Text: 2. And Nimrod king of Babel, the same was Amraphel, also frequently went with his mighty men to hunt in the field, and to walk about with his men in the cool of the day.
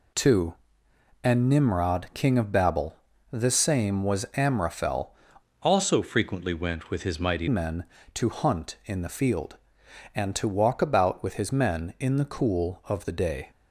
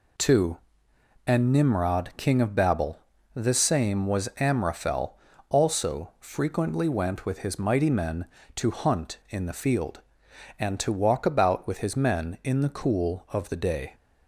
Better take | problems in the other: second | changes voice from "also" to "mighty"; from 5.6 to 7.4 s; 1.8 s long

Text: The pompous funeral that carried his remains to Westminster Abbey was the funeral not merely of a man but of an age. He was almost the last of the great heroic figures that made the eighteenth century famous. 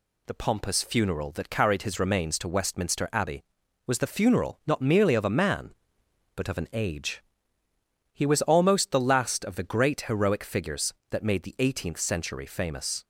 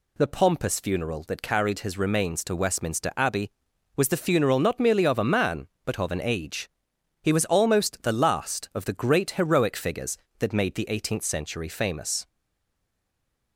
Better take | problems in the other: first | stays silent after the last word; noticeable; from 12.2 s on; 1.3 s long

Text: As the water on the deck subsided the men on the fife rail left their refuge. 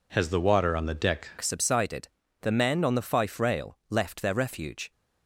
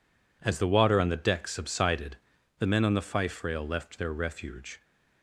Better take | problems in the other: second | changes voice at "subsided"; from 1.4 s on; 3.5 s long // pauses between "subsided" and "the"; slight; at 2.0 s; 0.34 s long; also in the second

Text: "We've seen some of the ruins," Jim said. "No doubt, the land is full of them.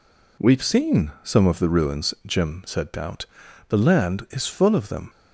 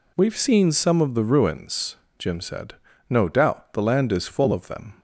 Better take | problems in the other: second | skips "No"; at 2.9 s

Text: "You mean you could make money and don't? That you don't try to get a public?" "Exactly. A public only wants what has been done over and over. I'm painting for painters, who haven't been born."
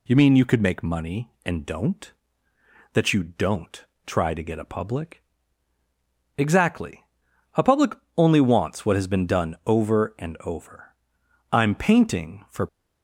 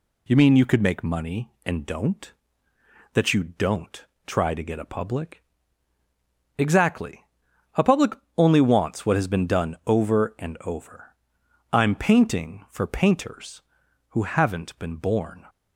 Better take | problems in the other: second | pauses between "don't" and "try"; slight; at 3.8 s; 0.22 s long; slight in the second // pauses between "public" and "only"; slight; at 7.9 s; 0.24 s long; slight in the second // stops before "painters who haven't been born"; at 12.6 s

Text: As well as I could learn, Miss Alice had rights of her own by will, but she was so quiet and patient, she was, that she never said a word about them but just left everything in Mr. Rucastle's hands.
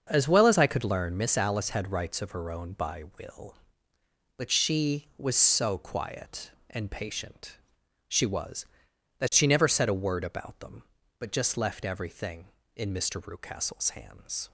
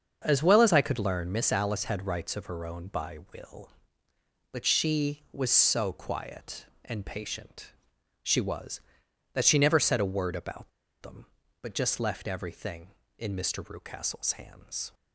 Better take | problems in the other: first | starts louder than the rest; until 1.2 s; 6.5 dB; also in the first // pauses between "about" and "them"; slight; at 10.7 s; 0.31 s long

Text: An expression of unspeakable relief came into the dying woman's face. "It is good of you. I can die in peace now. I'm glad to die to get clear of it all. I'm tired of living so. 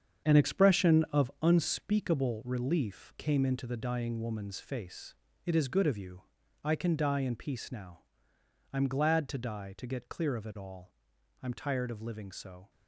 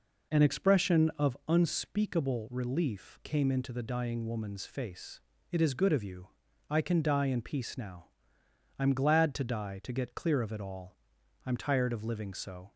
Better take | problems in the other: second | gets quieter; strong; throughout; 10 dB

